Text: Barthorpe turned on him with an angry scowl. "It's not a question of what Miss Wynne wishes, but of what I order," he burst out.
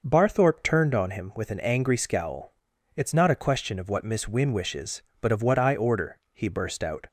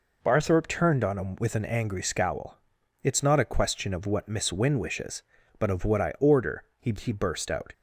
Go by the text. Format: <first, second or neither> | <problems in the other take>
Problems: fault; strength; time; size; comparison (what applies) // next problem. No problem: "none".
first | says "he" twice; at 6.9 s